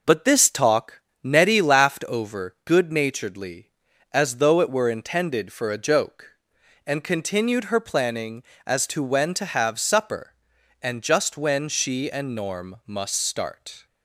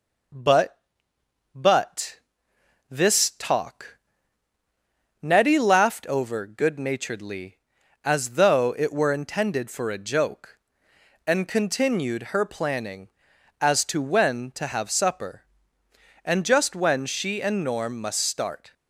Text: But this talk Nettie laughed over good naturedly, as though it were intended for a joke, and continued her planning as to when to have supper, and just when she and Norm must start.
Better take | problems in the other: first | says "But" twice; at 1.5 s // pauses between "talk" and "Nettie"; at 3.9 s; 1.2 s long; slight in the first

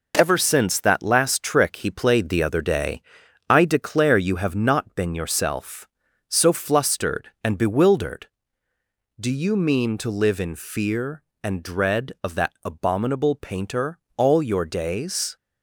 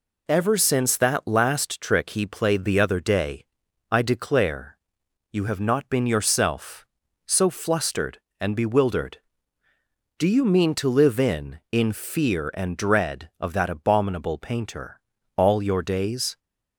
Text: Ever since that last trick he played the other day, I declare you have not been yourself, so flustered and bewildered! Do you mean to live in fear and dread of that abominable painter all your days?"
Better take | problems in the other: first | pauses between "declare" and "you"; noticeable; at 4.7 s; 0.54 s long // says "in" twice; at 11.7 s // pauses between "painter" and "all"; at 14.9 s; 0.38 s long; slight in the first

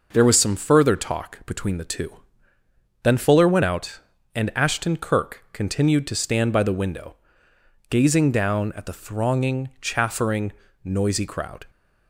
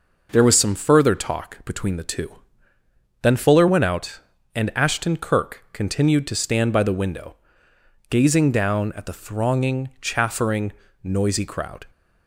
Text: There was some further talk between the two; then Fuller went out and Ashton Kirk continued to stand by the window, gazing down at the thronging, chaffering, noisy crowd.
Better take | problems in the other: neither | none

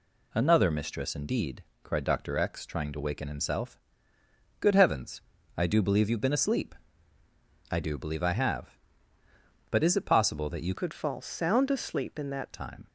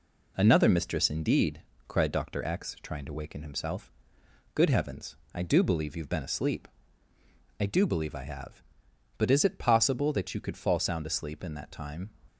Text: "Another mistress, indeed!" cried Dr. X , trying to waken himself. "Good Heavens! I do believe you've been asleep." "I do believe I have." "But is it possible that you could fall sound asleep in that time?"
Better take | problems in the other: second | changes voice from "could" to "that"; from 10.7 to 12.5 s; 1.8 s long

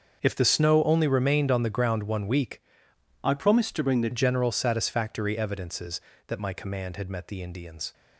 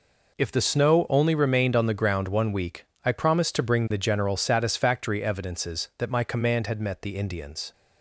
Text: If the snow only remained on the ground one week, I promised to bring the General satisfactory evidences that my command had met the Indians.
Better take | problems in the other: second | starts louder than the rest; until 1.2 s; 6.5 dB // changes voice from "I" to "the"; from 3.2 to 4.1 s; 0.9 s long

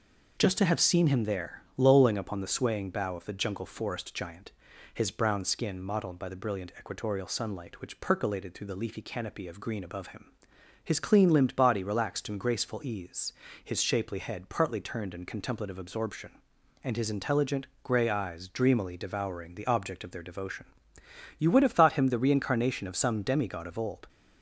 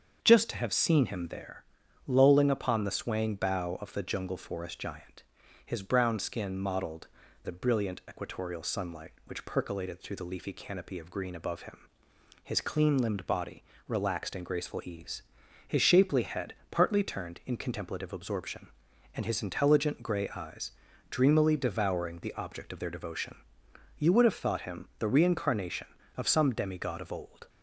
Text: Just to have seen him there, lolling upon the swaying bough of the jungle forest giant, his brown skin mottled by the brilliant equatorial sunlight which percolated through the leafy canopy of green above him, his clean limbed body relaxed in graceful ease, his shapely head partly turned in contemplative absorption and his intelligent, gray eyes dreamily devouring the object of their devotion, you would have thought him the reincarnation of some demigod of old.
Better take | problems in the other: first | starts louder than the rest; until 1.2 s; 7 dB // skips "by"; at 7.2 s // pauses between "body" and "relaxed"; slight; at 13.6 s; 0.24 s long // pauses between "head" and "partly"; slight; at 16.5 s; 0.16 s long // pauses between "eyes" and "dreamily"; at 20.7 s; 0.40 s long

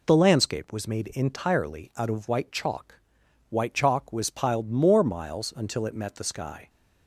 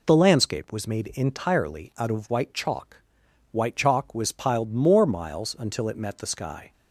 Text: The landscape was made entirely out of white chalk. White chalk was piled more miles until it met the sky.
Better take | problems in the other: neither | none

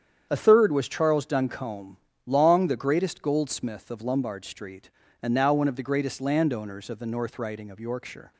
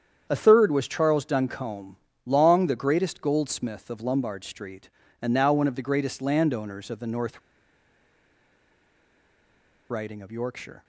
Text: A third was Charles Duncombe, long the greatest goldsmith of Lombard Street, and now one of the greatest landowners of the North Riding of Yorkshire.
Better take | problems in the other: first | starts louder than the rest; strong; until 1.3 s; 8.5 dB; strong in the first // pauses between "North" and "Riding"; strong; at 7.3 s; 2.5 s long

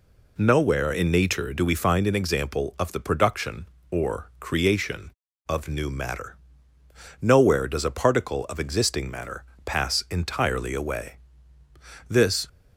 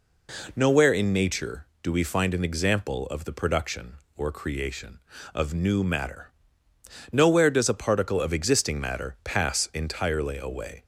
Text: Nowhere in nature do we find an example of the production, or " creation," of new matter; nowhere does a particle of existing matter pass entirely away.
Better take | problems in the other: second | pauses between "matter" and "pass"; slight; at 9.4 s; 0.18 s long // goes on to say "This"; slight; from 12.0 s on; 0.40 s long

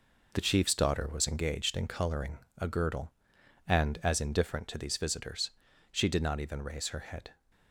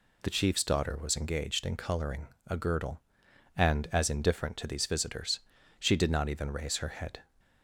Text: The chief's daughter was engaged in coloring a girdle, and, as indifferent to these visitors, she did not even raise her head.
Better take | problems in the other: second | gets quieter; throughout; 7 dB // pauses between "coloring" and "a"; slight; at 2.3 s; 0.18 s long; slight in the second

